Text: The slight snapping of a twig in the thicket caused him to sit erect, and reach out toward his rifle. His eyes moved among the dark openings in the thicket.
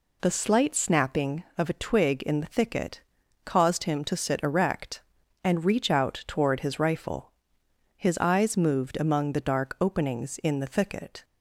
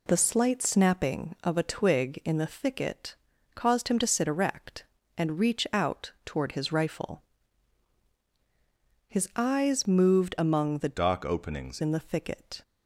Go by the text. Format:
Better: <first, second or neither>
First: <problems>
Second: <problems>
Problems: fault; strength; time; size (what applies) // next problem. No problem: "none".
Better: first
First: pauses between "thicket" and "caused"; noticeable; at 2.9 s; 0.46 s long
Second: pauses between "thicket" and "caused"; at 3.1 s; 0.38 s long // changes voice from "dark" to "openings"; from 10.9 to 11.7 s; 0.8 s long